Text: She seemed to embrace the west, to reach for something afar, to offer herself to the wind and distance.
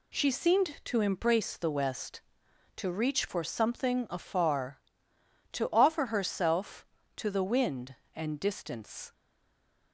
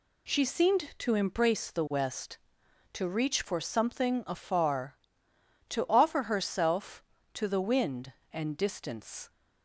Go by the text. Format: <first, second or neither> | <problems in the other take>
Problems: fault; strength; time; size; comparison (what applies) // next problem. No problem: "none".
second | stays silent after the last word; slight; from 9.1 s on; 0.8 s long